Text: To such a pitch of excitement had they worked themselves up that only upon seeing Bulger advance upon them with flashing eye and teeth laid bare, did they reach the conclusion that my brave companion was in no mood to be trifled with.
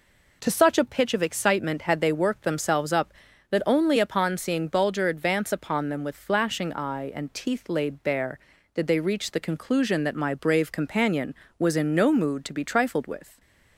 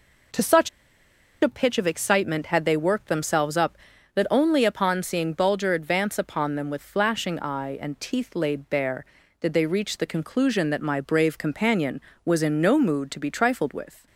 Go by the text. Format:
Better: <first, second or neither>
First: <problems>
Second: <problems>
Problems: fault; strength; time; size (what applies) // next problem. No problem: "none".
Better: first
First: none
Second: pauses between "such" and "a"; noticeable; at 0.6 s; 0.72 s long